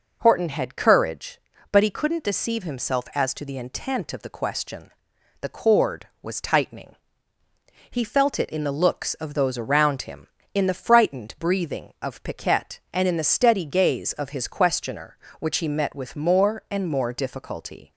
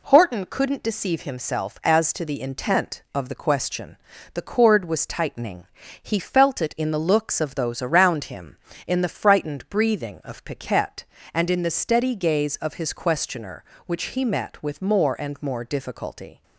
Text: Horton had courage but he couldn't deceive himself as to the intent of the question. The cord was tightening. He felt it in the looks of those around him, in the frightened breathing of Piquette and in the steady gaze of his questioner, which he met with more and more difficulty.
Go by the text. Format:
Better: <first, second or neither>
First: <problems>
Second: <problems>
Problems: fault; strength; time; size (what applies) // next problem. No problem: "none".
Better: first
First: none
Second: skips "had courage but he"; at 0.4 s